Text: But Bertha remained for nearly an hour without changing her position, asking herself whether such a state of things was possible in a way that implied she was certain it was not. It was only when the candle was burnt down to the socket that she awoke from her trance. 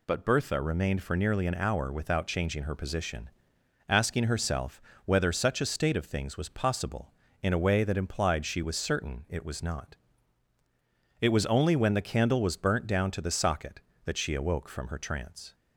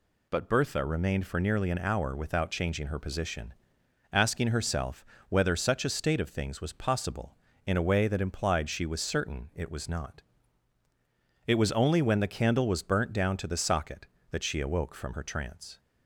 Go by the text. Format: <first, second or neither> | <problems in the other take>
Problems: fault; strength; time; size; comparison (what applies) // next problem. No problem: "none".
neither | pauses between "herself" and "whether"; slight; the same in both